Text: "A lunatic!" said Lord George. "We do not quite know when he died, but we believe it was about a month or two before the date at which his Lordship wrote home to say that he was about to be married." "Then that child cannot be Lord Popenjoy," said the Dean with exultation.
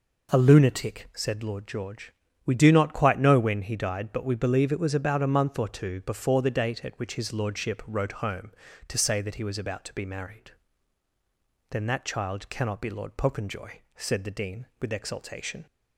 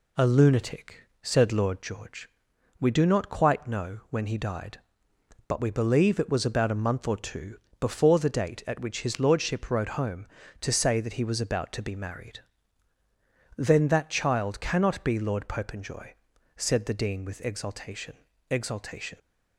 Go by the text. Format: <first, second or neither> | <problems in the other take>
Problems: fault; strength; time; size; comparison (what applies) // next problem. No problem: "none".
first | pauses between "two" and "before"; slight; at 7.5 s; 0.22 s long // says "exultation" twice; at 18.5 s